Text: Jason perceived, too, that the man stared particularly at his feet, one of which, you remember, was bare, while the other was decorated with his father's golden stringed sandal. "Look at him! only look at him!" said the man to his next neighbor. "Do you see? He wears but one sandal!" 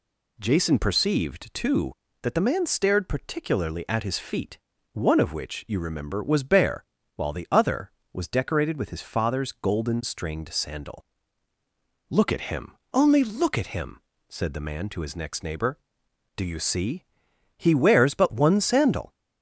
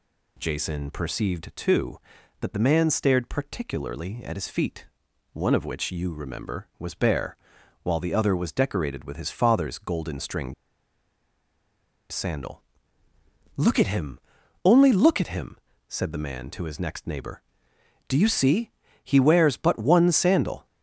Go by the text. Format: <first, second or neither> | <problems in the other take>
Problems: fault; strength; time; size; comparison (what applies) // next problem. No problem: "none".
first | pauses between "stringed" and "sandal"; strong; at 10.5 s; 1.5 s long